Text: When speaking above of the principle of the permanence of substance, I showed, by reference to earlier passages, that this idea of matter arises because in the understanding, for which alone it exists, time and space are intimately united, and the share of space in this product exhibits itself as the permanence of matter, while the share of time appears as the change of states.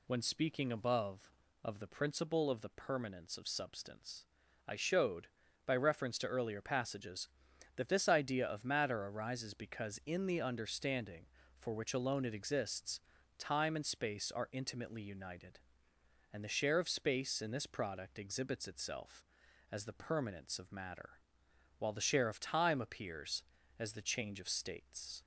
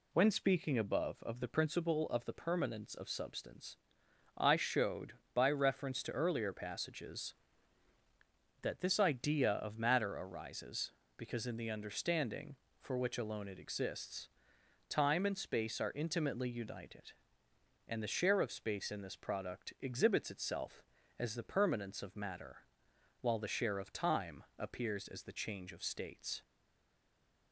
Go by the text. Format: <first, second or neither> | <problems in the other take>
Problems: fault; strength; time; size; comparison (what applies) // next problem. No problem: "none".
first | pauses between "time" and "appears"; slight; at 24.4 s; 0.16 s long // stays silent after the last word; from 26.4 s on; 1.1 s long